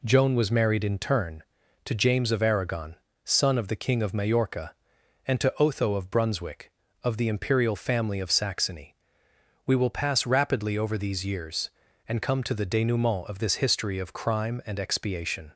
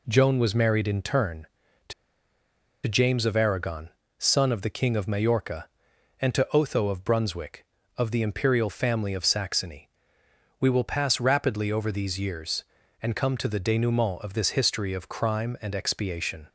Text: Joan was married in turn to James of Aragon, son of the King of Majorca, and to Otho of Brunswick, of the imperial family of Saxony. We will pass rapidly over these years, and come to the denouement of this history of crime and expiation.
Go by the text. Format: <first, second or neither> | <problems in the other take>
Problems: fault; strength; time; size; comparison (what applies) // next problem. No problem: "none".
first | pauses between "to" and "James"; noticeable; at 1.9 s; 0.93 s long